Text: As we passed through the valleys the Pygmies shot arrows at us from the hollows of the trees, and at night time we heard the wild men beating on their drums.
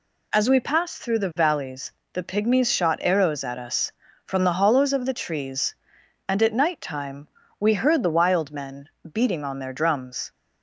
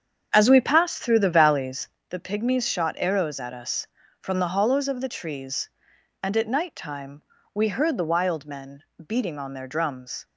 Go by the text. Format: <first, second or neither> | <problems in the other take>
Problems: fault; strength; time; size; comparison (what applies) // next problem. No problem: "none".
first | starts louder than the rest; strong; until 2.0 s; 7.5 dB // pauses between "valleys" and "the"; slight; at 1.8 s; 0.22 s long; slight in the first // pauses between "time" and "we"; slight; at 7.2 s; 0.32 s long; slight in the first // pauses between "men" and "beating"; slight; at 8.8 s; 0.24 s long; slight in the first